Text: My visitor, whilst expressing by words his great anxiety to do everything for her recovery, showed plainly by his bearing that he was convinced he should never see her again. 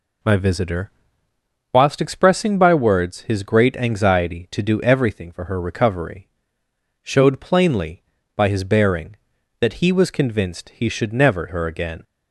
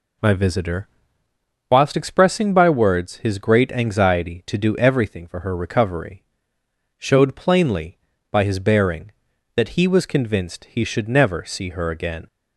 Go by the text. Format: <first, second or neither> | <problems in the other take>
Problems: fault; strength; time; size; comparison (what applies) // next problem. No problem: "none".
second | skips "see"; at 11.4 s